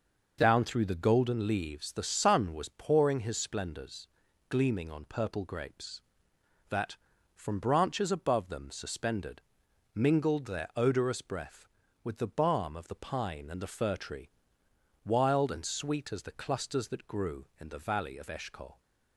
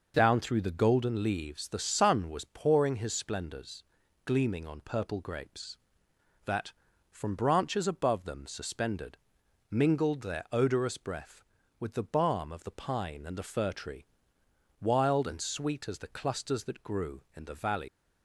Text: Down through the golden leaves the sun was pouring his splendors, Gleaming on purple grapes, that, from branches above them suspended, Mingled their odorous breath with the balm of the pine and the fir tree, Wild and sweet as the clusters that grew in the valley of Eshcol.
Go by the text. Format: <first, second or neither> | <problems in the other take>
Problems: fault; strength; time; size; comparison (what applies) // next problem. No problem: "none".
first | stops before "of Eshcol"; at 17.8 s